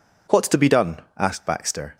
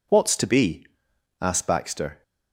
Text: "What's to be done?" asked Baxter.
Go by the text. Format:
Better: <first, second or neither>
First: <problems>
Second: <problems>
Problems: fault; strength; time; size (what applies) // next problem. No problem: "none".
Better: first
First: none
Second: skips "done"; at 1.1 s